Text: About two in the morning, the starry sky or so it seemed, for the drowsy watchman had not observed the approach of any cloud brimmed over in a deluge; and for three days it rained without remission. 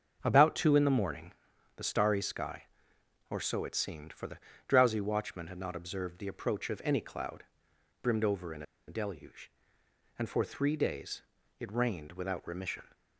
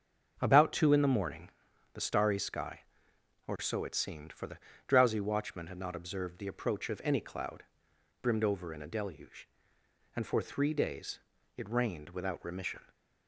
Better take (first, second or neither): second